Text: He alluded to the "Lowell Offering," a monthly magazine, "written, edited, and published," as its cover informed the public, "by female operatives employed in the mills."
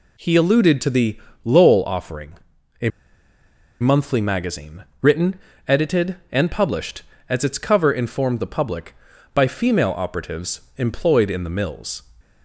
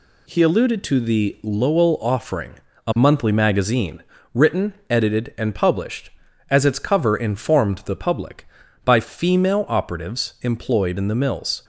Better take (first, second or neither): second